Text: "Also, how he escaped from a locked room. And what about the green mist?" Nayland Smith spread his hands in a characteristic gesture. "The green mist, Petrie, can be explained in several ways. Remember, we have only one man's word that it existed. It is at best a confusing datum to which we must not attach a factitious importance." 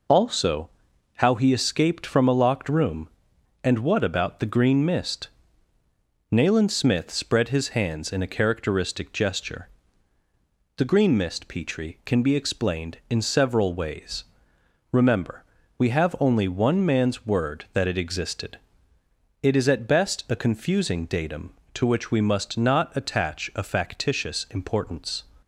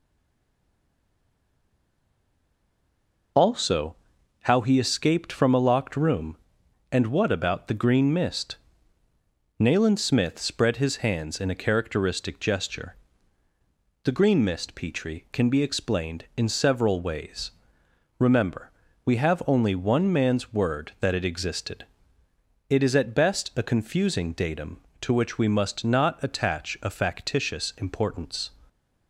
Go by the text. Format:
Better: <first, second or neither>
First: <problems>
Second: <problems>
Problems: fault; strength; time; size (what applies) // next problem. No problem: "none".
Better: first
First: none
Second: stays silent before the first word; strong; until 3.3 s; 3.3 s long